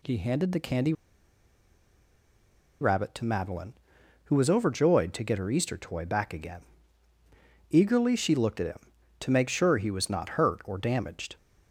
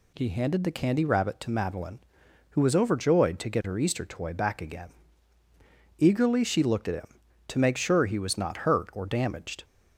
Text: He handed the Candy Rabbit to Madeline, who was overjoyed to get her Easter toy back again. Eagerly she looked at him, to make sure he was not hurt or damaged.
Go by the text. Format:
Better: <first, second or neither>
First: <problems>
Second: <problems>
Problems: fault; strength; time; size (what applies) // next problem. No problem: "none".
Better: second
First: pauses between "Candy" and "Rabbit"; strong; at 0.9 s; 1.8 s long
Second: none